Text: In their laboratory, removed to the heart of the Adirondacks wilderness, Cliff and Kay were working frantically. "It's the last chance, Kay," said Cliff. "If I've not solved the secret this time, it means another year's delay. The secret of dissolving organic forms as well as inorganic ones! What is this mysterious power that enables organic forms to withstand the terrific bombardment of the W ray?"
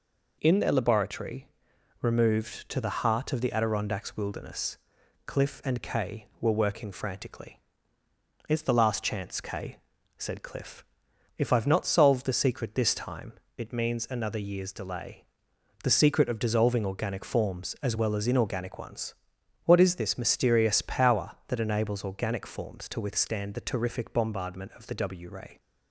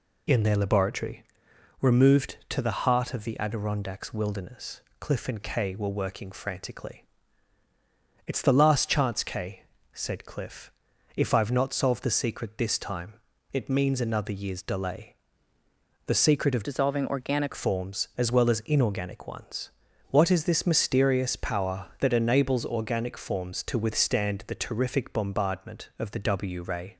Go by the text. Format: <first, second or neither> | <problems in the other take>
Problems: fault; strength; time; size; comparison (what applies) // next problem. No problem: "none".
first | changes voice from "dissolving" to "organic"; from 16.6 to 17.5 s; 0.9 s long